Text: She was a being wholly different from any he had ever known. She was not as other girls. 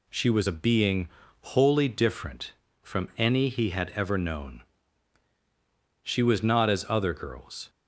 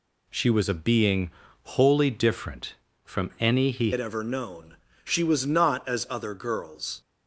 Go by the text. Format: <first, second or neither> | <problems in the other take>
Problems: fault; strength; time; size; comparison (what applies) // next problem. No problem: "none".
first | pauses between "being" and "wholly"; slight; at 1.2 s; 0.34 s long; slight in the first // changes voice at "had"; from 3.9 s on; 3.1 s long